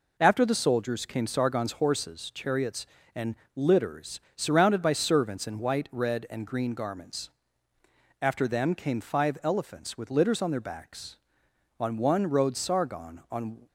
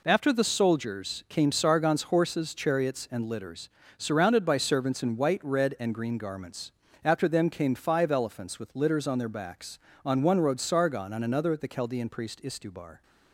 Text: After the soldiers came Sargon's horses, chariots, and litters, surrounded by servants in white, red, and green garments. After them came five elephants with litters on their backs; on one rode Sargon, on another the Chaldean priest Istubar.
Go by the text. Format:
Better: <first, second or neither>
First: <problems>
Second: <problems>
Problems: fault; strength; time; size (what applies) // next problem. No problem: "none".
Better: second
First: pauses between "and" and "litters"; slight; at 3.3 s; 0.20 s long // stops before "another the Chaldean priest Istubar"; at 13.6 s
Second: none